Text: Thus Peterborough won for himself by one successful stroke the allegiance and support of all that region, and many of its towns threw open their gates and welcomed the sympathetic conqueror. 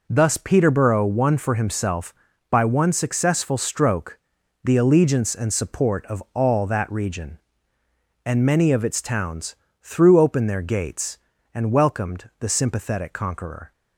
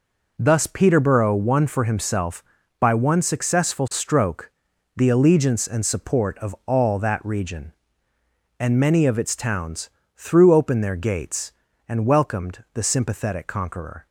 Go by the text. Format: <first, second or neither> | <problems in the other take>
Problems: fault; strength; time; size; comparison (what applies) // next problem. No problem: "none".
neither | pauses between "stroke" and "the"; noticeable; the same in both // pauses between "towns" and "threw"; slight; the same in both